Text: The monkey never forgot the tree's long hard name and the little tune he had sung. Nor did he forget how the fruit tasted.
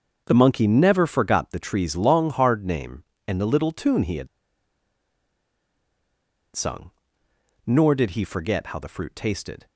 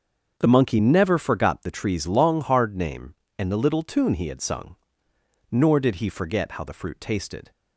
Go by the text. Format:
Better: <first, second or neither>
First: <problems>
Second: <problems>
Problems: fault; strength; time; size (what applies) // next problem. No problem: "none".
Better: second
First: starts louder than the rest; until 1.2 s; 6.5 dB // pauses between "had" and "sung"; strong; at 4.2 s; 2.2 s long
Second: starts louder than the rest; until 1.3 s; 6.5 dB